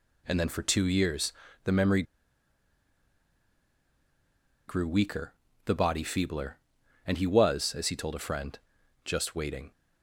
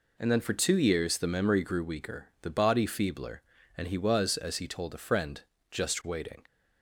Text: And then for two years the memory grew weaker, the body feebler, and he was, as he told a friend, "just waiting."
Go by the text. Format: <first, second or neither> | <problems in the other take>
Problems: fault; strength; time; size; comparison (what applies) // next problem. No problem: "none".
second | pauses between "years" and "the"; slight; at 1.3 s; 0.32 s long // pauses between "memory" and "grew"; strong; at 2.0 s; 2.6 s long